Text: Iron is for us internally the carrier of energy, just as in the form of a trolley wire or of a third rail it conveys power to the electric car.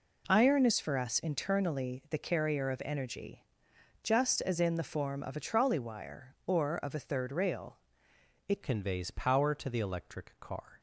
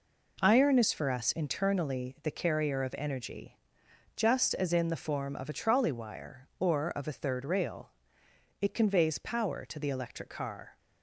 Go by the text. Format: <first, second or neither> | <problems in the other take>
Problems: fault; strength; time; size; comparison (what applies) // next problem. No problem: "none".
second | pauses between "rail" and "it"; noticeable; at 7.7 s; 0.70 s long; noticeable in the second // changes voice at "conveys"; from 8.6 s on; 2.1 s long